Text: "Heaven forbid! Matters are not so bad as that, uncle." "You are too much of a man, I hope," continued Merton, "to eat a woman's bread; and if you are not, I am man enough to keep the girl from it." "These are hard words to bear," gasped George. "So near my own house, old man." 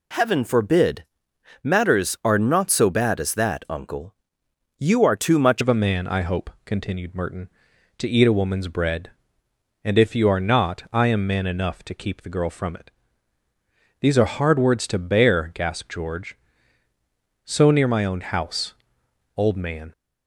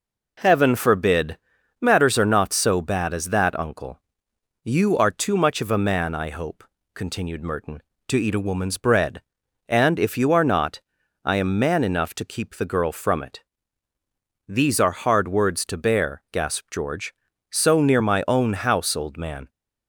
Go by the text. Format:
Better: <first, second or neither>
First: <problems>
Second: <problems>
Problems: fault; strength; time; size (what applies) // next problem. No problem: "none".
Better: second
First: changes voice at "of"; from 5.5 s on; 14.4 s long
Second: none